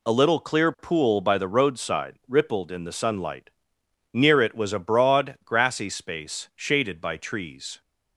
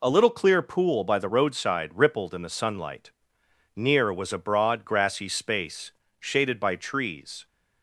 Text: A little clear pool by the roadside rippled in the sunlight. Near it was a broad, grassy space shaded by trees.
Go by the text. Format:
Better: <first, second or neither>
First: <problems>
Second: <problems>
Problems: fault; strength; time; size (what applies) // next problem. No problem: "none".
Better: first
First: none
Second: skips "it"; at 4.1 s // pauses between "space" and "shaded"; slight; at 5.9 s; 0.30 s long